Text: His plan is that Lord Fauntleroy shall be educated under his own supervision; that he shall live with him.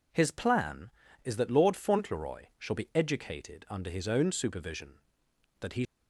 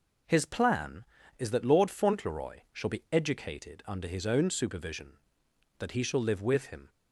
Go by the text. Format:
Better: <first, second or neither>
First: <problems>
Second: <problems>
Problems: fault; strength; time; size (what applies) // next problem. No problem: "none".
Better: second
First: stops before "shall live with him"; at 5.8 s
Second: none